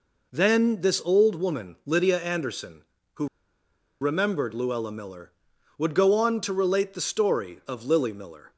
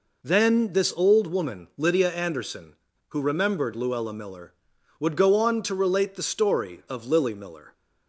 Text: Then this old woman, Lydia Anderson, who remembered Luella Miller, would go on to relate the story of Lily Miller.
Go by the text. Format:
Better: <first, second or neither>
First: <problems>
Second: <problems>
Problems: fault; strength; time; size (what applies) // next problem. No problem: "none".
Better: second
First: pauses between "who" and "remembered"; noticeable; at 3.2 s; 0.75 s long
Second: none